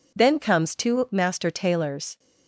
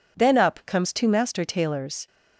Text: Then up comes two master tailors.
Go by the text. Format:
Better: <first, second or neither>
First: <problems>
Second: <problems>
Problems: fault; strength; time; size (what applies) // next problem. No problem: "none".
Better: second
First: skips "up"; at 0.3 s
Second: none